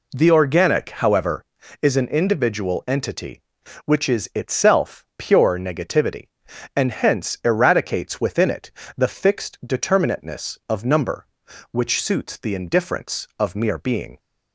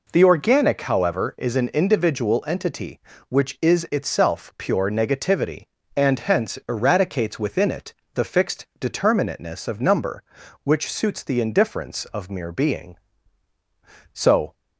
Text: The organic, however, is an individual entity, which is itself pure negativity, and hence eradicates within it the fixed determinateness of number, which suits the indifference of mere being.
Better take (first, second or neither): first